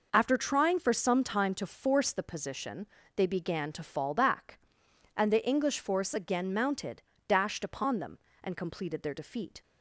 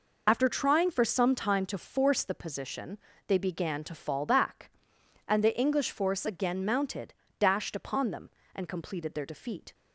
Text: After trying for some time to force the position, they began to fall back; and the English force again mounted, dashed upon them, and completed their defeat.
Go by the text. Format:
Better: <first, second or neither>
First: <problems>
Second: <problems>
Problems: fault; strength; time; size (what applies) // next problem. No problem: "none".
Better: first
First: none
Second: loses the start of "After"; at 0.2 s; 40 ms